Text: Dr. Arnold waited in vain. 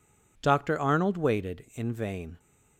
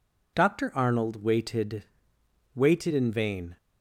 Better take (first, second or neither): first